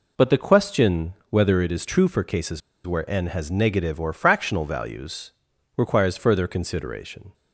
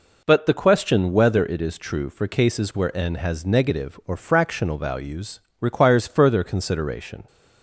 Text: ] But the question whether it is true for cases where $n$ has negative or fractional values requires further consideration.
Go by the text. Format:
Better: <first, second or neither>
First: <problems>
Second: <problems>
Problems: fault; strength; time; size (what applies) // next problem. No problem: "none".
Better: second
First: pauses between "question" and "whether"; slight; at 1.1 s; 0.16 s long // pauses between "cases" and "where"; slight; at 2.6 s; 0.26 s long // pauses between "values" and "requires"; at 5.3 s; 0.42 s long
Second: pauses between "values" and "requires"; slight; at 5.3 s; 0.20 s long